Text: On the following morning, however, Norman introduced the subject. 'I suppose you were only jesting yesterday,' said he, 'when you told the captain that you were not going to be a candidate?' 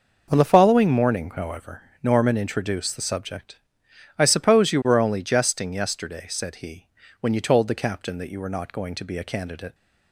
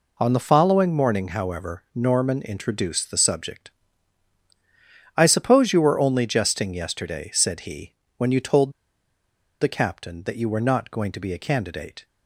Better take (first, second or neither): first